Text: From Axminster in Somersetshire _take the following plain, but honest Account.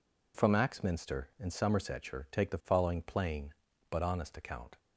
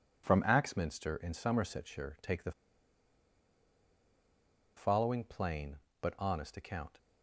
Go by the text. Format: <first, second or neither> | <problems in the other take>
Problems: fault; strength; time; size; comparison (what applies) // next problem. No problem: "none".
first | pauses between "the" and "following"; strong; at 2.5 s; 2.2 s long